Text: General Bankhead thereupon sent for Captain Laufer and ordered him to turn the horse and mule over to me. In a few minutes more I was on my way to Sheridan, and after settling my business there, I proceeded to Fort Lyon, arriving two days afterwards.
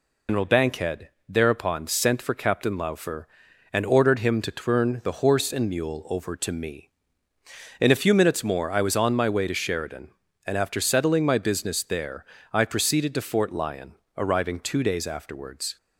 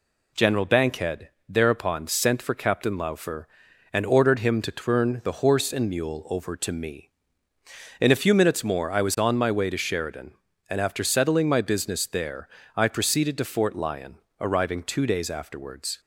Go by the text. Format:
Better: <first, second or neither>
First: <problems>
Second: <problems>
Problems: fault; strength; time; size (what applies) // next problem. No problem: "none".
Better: second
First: loses the start of "General"; at 0.2 s; 150 ms // pauses between "Bankhead" and "thereupon"; slight; at 1.0 s; 0.18 s long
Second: pauses between "Bankhead" and "thereupon"; slight; at 1.2 s; 0.18 s long